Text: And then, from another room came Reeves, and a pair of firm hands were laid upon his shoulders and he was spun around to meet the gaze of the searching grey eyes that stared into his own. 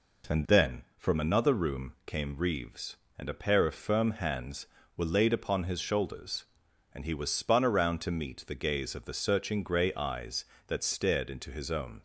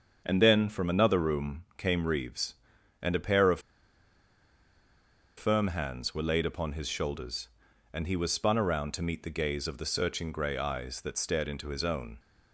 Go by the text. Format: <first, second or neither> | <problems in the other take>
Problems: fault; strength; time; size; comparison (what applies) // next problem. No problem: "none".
first | starts louder than the rest; strong; until 1.2 s; 7 dB // pauses between "of" and "firm"; strong; at 3.5 s; 1.7 s long